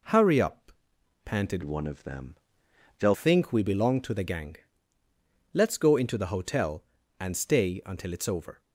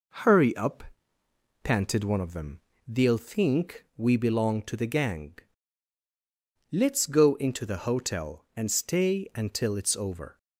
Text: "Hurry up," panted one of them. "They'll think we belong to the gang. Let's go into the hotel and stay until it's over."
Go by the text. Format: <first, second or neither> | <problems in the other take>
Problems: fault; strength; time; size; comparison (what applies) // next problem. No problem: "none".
second | changes voice from "one" to "They'll"; from 1.6 to 3.1 s; 1.5 s long